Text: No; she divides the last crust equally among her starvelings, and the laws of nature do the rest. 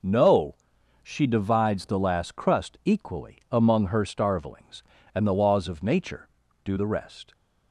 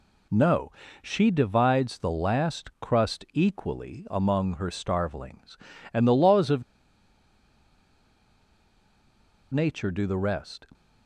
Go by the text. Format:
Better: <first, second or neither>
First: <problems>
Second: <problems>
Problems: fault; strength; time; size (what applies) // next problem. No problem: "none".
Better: first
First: none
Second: pauses between "of" and "nature"; strong; at 6.6 s; 2.9 s long